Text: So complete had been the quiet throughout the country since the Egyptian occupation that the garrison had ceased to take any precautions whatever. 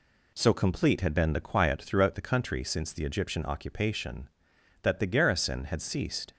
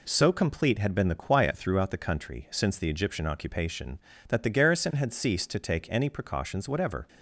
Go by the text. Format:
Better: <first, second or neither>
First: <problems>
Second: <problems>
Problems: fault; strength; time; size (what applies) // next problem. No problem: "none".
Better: second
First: stops before "to take any precautions whatever"; at 6.3 s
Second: none